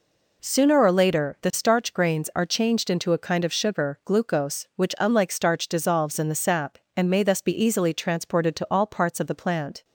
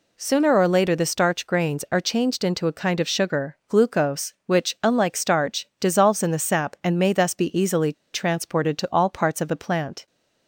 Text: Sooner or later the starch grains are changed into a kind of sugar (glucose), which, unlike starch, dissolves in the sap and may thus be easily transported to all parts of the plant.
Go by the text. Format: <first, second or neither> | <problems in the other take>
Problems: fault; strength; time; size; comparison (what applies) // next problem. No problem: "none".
first | pauses between "easily" and "transported"; slight; at 7.9 s; 0.20 s long